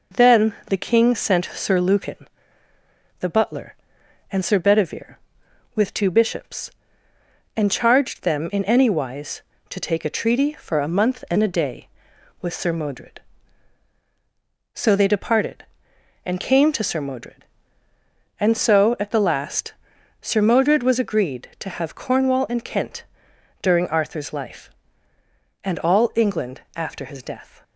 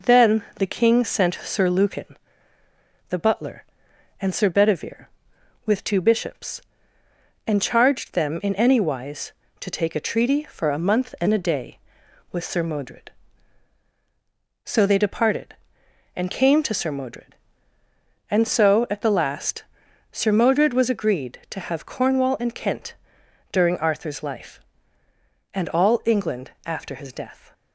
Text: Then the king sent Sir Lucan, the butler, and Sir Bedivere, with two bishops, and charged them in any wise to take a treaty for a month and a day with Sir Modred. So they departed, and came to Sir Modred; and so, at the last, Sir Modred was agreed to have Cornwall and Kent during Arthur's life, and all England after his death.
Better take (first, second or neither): neither